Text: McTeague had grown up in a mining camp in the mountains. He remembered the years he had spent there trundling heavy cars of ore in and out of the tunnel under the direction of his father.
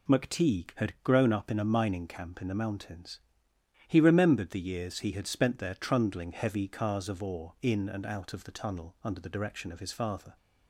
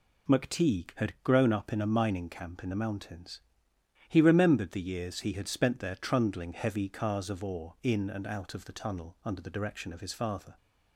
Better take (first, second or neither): neither